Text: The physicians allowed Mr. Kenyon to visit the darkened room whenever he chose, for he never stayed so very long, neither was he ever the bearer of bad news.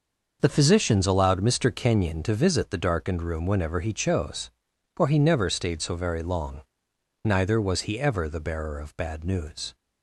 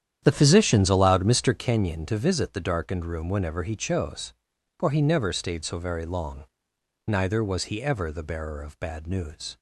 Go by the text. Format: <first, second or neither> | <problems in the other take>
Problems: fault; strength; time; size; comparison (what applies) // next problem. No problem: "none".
first | starts louder than the rest; strong; until 1.7 s; 9.5 dB